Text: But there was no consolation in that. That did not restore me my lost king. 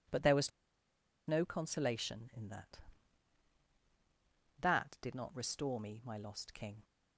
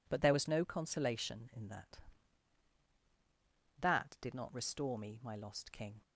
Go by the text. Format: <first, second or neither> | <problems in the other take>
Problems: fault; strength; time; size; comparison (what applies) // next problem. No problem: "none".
second | pauses between "was" and "no"; noticeable; at 0.5 s; 0.78 s long